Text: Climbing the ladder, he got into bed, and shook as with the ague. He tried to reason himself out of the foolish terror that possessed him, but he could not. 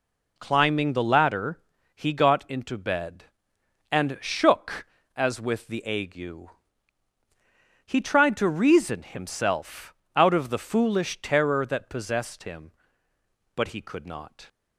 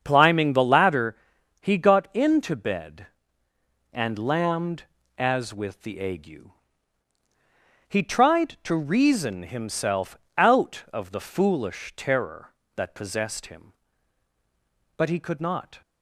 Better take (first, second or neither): first